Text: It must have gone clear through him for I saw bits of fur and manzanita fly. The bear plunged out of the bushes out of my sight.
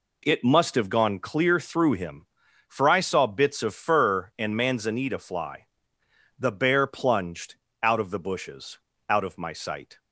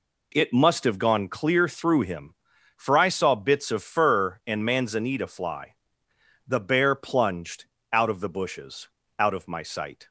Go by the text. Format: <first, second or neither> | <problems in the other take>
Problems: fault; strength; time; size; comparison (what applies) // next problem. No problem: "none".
neither | pauses between "plunged" and "out"; slight; the same in both // pauses between "bushes" and "out"; slight; the same in both